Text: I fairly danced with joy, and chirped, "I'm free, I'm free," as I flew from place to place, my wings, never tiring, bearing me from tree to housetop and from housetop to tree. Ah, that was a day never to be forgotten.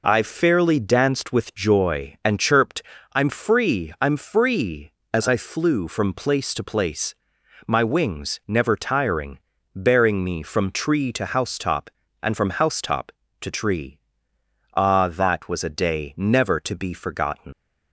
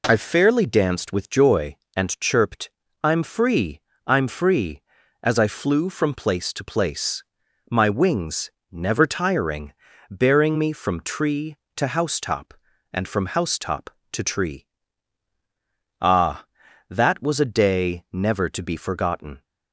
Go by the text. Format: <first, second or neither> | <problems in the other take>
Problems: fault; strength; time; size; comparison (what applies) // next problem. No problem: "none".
second | leaves "forgotten" unfinished; at 17.5 s; 115 ms